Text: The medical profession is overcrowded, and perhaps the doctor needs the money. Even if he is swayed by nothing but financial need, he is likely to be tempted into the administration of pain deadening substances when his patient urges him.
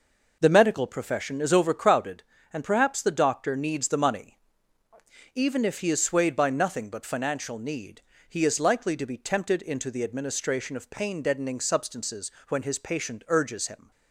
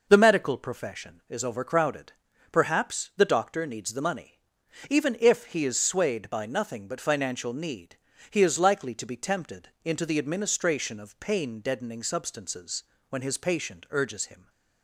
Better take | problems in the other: first | skips "and"; at 2.3 s // pauses between "substances" and "when"; slight; at 12.8 s; 0.26 s long; slight in the first

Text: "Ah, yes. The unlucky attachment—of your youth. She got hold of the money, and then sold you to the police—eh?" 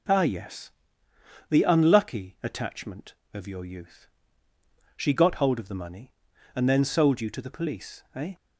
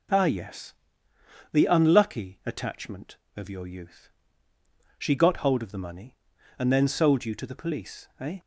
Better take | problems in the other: neither | none

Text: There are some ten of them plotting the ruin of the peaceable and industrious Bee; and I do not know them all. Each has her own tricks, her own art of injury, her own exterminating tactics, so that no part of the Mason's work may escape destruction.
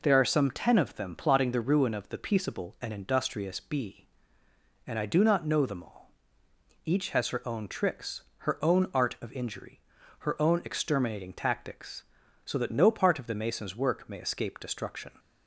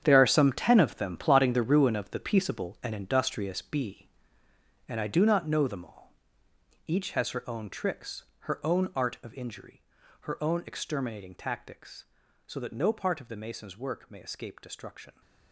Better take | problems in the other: first | gets quieter; strong; throughout; 13 dB

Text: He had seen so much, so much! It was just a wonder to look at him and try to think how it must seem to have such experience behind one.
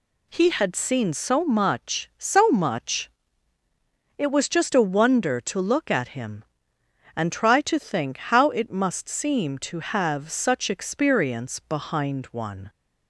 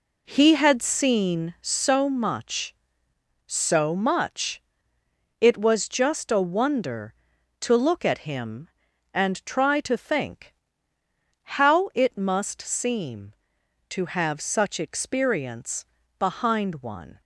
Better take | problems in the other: first | starts louder than the rest; slight; until 2.0 s; 2.5 dB // pauses between "think" and "how"; noticeable; at 10.5 s; 0.92 s long // pauses between "experience" and "behind"; slight; at 15.8 s; 0.34 s long

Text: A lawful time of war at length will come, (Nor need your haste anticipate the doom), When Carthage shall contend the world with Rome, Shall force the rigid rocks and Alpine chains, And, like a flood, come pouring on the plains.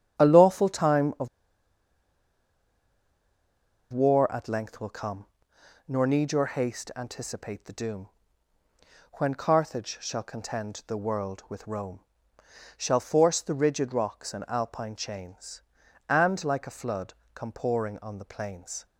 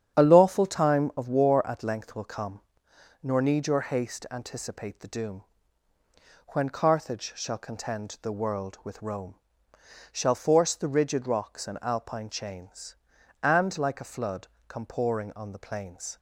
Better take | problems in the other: second | starts louder than the rest; strong; until 1.2 s; 9 dB; strong in the second // pauses between "of" and "war"; strong; at 1.2 s; 2.6 s long

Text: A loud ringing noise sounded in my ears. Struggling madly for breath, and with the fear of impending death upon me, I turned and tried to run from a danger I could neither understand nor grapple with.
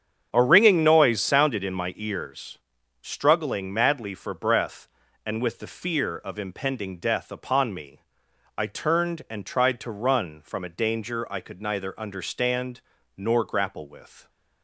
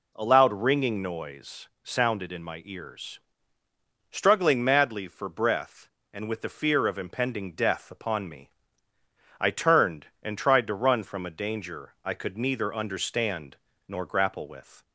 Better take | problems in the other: second | starts louder than the rest; strong; until 1.3 s; 8 dB // skips "loud"; at 0.4 s // pauses between "understand" and "nor"; at 12.7 s; 0.38 s long; slight in the second

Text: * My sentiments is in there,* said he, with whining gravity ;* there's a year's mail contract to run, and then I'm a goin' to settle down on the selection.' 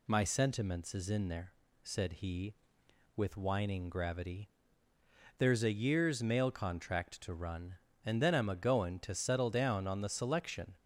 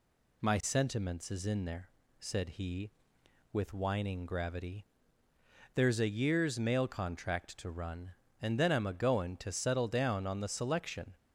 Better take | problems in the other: neither | none

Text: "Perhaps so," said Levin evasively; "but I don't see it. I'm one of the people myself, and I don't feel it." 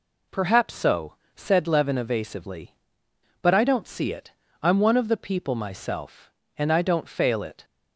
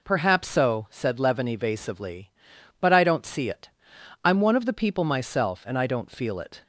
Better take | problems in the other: second | says "fail" for "feel"; at 7.0 s

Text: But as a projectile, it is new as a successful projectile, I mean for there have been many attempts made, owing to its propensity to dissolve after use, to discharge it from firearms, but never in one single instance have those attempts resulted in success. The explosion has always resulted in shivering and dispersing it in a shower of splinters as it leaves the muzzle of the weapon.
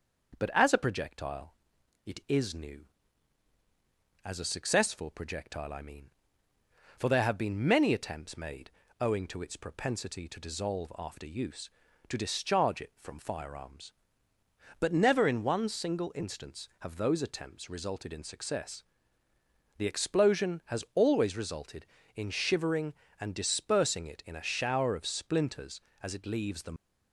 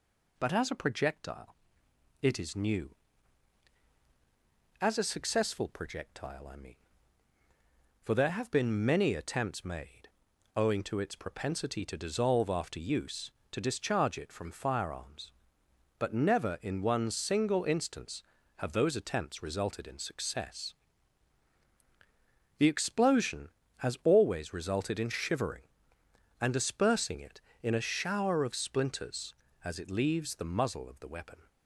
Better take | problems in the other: second | starts louder than the rest; noticeable; until 1.4 s; 6 dB // stops before "muzzle of the weapon"; at 26.7 s

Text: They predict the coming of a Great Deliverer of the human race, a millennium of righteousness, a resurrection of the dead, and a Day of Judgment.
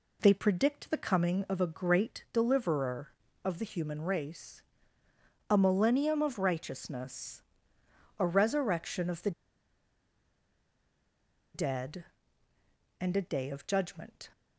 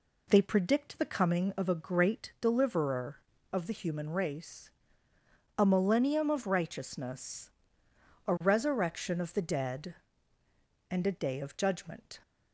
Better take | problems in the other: second | pauses between "the" and "dead"; strong; at 9.3 s; 2.2 s long

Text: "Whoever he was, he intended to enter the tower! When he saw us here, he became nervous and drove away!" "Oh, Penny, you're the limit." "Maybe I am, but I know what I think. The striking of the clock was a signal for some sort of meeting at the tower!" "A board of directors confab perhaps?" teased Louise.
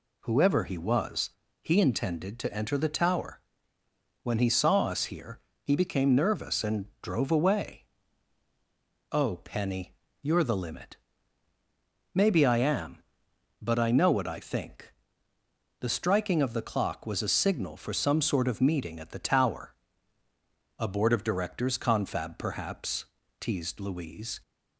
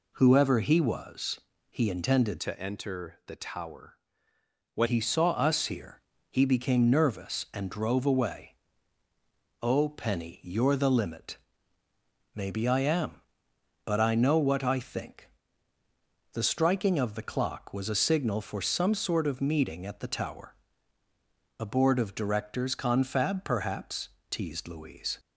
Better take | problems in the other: first | changes voice from "to" to "When"; from 2.3 to 4.8 s; 2.5 s long

